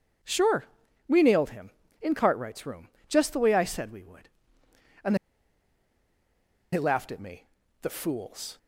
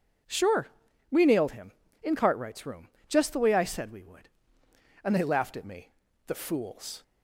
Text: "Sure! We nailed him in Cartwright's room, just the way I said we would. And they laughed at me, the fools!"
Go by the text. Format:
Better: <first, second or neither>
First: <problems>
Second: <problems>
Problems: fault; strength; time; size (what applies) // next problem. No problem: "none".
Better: second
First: pauses between "And" and "they"; strong; at 5.1 s; 1.5 s long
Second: none